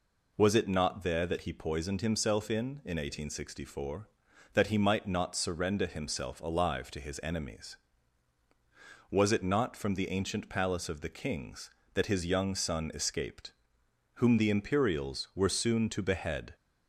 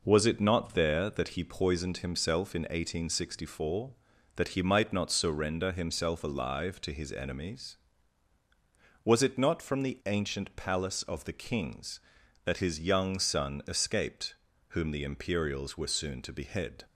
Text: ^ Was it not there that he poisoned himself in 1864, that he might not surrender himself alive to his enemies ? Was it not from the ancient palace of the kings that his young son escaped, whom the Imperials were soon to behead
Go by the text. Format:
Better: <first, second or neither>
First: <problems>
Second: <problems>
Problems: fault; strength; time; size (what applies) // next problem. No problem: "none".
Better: second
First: says "in" twice; at 2.8 s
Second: none